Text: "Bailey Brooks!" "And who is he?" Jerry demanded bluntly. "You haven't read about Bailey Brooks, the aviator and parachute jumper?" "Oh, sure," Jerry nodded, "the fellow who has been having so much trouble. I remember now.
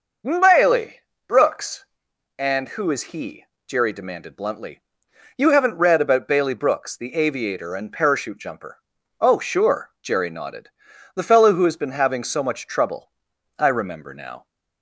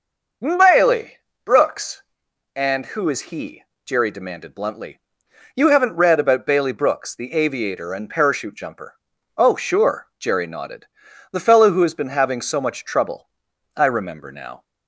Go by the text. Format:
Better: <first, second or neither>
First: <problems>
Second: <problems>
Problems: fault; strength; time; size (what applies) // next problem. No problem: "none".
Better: neither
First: pauses between "Bailey" and "Brooks"; slight; at 1.0 s; 0.26 s long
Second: pauses between "Bailey" and "Brooks"; slight; at 1.1 s; 0.26 s long